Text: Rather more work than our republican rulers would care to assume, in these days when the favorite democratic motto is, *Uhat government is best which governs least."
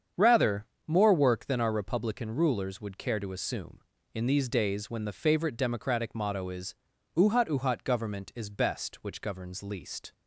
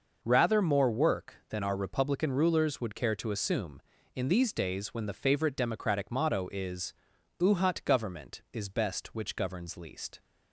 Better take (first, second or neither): second